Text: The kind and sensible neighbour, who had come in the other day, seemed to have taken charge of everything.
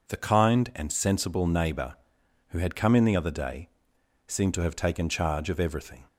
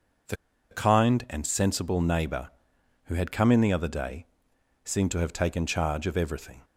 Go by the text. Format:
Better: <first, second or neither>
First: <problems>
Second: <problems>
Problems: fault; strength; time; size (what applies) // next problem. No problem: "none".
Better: first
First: none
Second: pauses between "The" and "kind"; slight; at 0.3 s; 0.35 s long